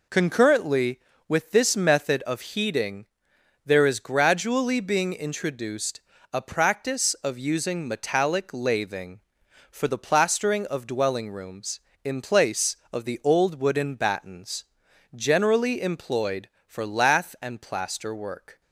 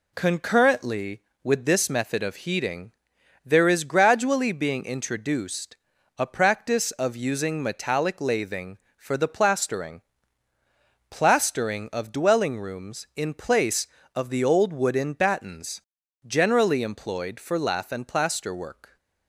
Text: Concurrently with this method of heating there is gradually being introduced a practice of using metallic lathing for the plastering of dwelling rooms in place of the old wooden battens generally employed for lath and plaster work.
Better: first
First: pauses between "heating" and "there"; noticeable; at 3.0 s; 0.58 s long // pauses between "introduced" and "a"; slight; at 6.0 s; 0.32 s long // pauses between "battens" and "generally"; noticeable; at 14.6 s; 0.52 s long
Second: pauses between "heating" and "there"; noticeable; at 2.9 s; 0.52 s long // pauses between "introduced" and "a"; at 5.7 s; 0.42 s long // says "plastering" twice; at 11.1 s // pauses between "battens" and "generally"; at 15.8 s; 0.44 s long

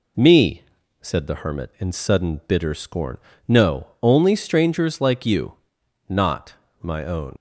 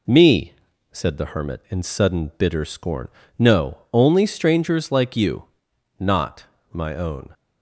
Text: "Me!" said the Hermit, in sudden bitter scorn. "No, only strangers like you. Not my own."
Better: second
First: pauses between "Not" and "my"; slight; at 6.5 s; 0.28 s long // leaves "own" unfinished; at 7.3 s; 60 ms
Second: pauses between "Not" and "my"; slight; at 6.4 s; 0.28 s long

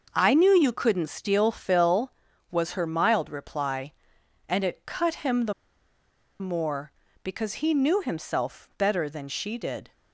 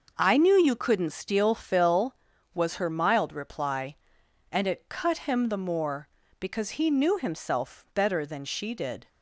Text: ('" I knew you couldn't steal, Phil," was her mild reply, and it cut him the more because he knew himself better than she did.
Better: second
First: starts louder than the rest; noticeable; until 1.1 s; 6 dB // pauses between "the" and "more"; noticeable; at 5.5 s; 0.87 s long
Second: starts louder than the rest; noticeable; until 1.1 s; 6 dB

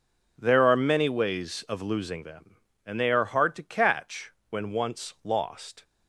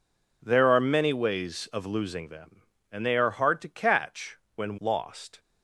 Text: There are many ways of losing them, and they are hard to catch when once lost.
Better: first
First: pauses between "catch" and "when"; slight; at 4.3 s; 0.18 s long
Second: pauses between "catch" and "when"; slight; at 4.3 s; 0.18 s long // skips "once"; at 4.7 s

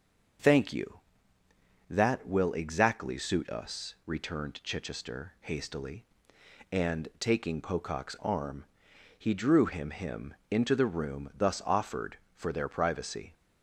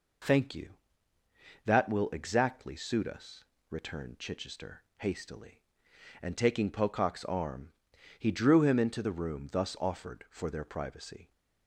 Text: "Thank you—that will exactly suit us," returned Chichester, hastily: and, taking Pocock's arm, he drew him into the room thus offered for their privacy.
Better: second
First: says "him" twice; at 9.8 s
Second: none

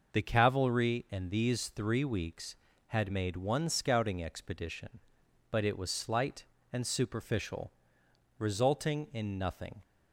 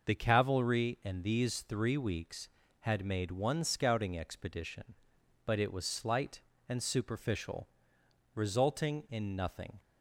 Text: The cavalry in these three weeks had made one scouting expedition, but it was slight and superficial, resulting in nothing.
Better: neither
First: none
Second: none

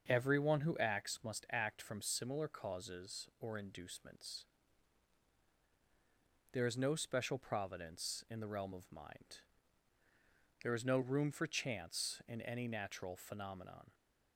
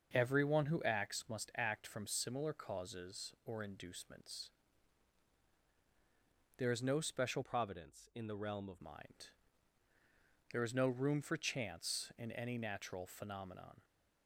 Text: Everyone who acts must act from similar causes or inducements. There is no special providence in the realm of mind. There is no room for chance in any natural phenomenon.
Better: first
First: starts louder than the rest; until 1.1 s; 6.5 dB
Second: starts louder than the rest; until 1.1 s; 6.5 dB // changes voice from "providence" to "of"; from 7.4 to 8.8 s; 1.4 s long

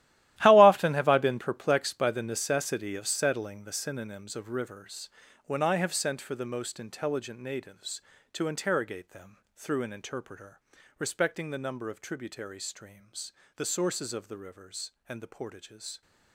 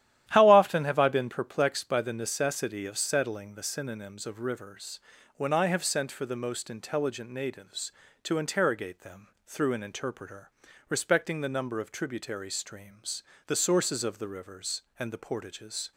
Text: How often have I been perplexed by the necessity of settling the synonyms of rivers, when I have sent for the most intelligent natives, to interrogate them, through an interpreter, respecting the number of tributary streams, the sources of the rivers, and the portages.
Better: second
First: gets quieter; strong; throughout; 14.5 dB // starts louder than the rest; strong; until 1.4 s; 14.5 dB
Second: starts louder than the rest; strong; until 1.3 s; 12 dB

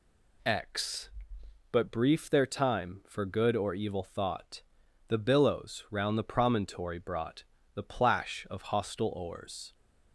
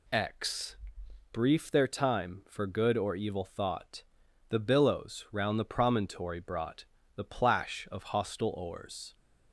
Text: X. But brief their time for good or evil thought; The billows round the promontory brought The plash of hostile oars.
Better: first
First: pauses between "brought" and "The"; slight; at 7.4 s; 0.30 s long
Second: skips "But"; at 1.0 s // pauses between "brought" and "The"; slight; at 6.8 s; 0.30 s long

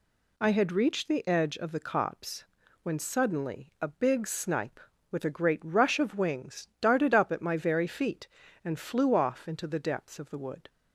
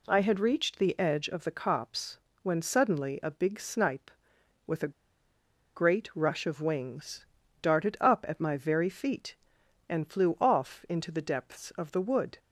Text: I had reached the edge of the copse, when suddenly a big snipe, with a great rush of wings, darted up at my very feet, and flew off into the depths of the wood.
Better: first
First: none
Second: pauses between "a" and "great"; noticeable; at 4.9 s; 0.84 s long

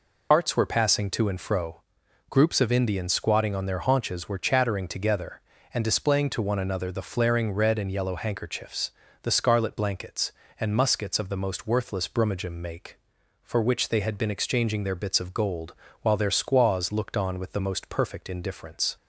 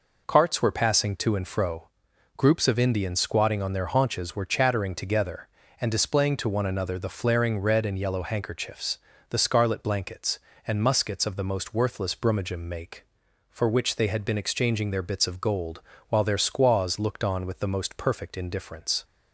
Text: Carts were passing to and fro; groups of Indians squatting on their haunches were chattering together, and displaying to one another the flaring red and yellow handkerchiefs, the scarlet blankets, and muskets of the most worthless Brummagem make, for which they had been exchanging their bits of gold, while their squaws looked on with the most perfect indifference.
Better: second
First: loses the start of "Carts"; at 0.3 s; 95 ms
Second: none

